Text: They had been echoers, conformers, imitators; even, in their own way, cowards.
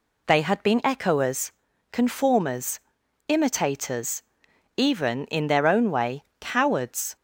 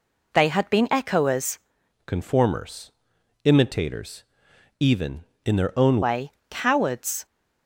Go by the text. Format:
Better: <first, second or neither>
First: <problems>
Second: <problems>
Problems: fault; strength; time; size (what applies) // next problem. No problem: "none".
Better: first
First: none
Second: changes voice from "conformers" to "own"; from 2.0 to 6.0 s; 4.0 s long